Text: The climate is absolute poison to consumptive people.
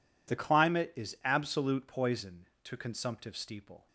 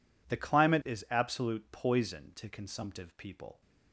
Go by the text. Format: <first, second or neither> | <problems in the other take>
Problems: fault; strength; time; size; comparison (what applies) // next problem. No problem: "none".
second | says "steeple" for "people"; at 3.3 s